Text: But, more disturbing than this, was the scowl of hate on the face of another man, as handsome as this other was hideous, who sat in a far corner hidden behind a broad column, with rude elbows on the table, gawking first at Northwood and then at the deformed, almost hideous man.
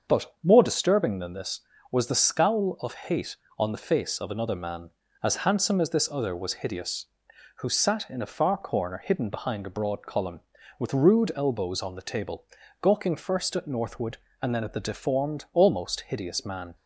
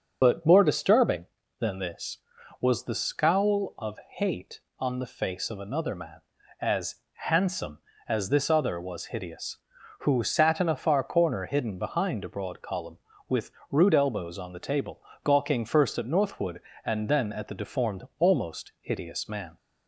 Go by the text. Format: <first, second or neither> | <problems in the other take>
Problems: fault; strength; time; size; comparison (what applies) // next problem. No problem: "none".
first | loses the start of "But"; at 0.2 s; 60 ms // starts louder than the rest; until 1.2 s; 6.5 dB; also in the first // pauses between "as" and "handsome"; slight; at 6.9 s; 0.18 s long // pauses between "with" and "rude"; slight; at 13.5 s; 0.20 s long